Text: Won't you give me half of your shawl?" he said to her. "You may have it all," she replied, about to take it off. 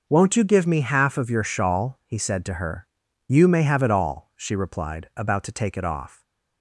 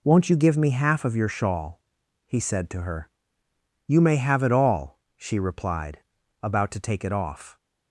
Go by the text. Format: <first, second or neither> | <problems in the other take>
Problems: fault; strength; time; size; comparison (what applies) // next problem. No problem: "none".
neither | none